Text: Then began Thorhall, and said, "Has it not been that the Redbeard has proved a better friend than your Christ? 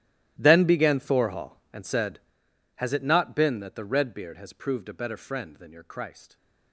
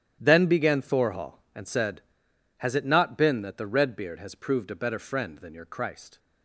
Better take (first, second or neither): second